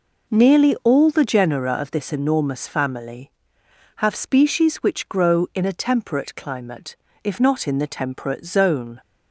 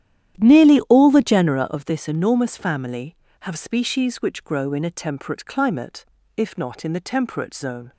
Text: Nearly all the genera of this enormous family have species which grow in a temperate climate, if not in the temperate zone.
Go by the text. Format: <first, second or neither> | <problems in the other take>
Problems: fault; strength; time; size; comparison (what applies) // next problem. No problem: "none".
first | starts louder than the rest; strong; until 1.6 s; 11 dB